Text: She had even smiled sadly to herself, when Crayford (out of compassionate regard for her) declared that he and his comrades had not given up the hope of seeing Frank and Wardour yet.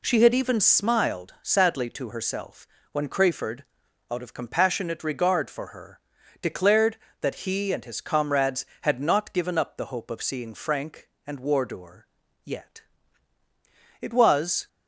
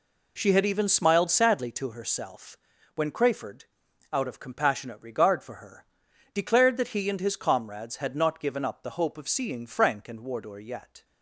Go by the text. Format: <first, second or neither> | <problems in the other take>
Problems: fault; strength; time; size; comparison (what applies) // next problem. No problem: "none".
second | pauses between "Wardour" and "yet"; at 12.0 s; 0.38 s long // goes on to say "It was"; noticeable; from 14.0 s on; 0.66 s long